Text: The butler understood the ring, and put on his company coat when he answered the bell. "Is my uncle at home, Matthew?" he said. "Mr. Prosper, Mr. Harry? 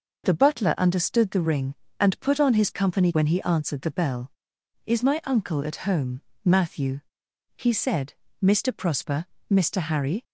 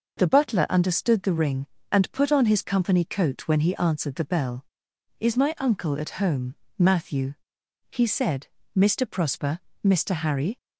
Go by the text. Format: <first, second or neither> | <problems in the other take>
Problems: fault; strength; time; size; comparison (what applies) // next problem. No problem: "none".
second | skips "coat"; at 3.1 s